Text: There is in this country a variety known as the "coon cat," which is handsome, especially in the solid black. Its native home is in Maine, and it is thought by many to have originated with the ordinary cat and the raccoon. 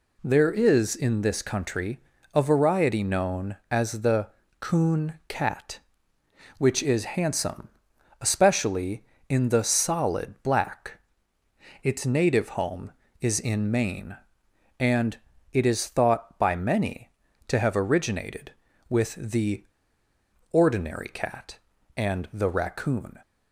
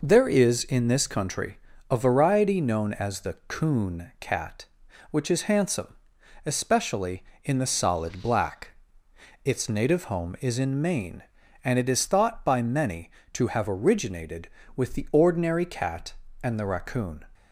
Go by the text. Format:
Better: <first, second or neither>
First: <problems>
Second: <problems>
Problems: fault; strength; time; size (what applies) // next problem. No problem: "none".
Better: second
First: pauses between "country" and "a"; slight; at 2.0 s; 0.34 s long // pauses between "the" and "coon"; slight; at 4.2 s; 0.34 s long // pauses between "and" and "it"; at 15.1 s; 0.38 s long // pauses between "the" and "ordinary"; noticeable; at 19.6 s; 0.87 s long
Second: pauses between "country" and "a"; slight; at 1.5 s; 0.34 s long